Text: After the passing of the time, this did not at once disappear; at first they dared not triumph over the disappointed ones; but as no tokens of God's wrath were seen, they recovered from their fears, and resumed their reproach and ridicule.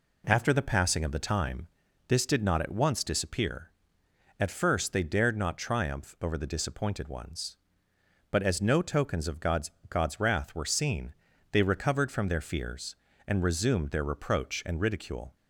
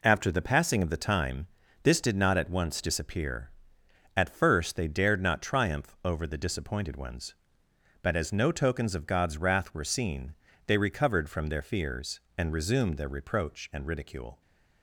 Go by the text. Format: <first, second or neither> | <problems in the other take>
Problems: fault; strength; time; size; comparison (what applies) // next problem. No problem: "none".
second | says "God's" twice; at 9.8 s